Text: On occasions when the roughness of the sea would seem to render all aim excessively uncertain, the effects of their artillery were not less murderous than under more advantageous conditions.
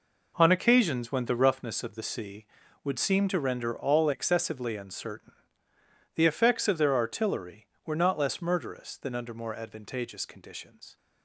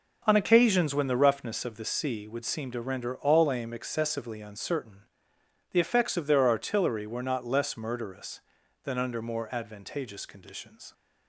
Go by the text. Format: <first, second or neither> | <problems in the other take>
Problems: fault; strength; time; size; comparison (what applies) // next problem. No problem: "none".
second | skips "aim"; at 4.1 s